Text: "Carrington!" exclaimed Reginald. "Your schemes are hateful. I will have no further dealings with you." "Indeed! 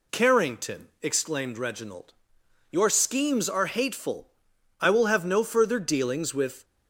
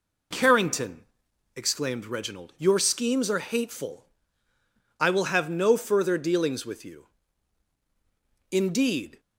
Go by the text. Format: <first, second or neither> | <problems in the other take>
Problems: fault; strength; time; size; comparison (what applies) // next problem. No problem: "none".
second | stops before "you Indeed"; at 6.6 s